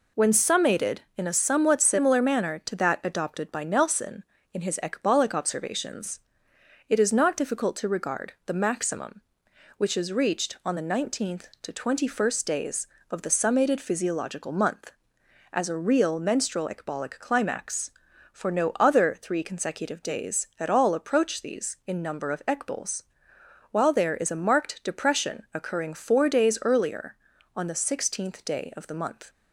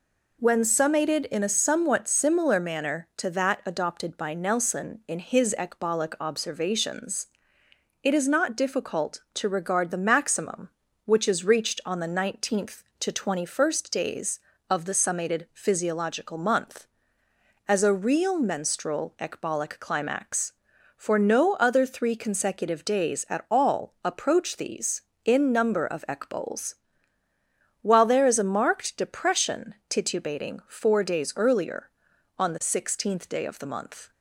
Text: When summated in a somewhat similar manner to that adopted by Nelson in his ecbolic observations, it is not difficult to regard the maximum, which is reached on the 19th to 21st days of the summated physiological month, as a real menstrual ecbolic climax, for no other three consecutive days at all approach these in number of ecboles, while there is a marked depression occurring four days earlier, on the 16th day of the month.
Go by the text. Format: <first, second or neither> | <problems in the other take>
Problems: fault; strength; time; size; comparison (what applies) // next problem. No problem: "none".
first | says "titubating" for "occurring"; at 29.8 s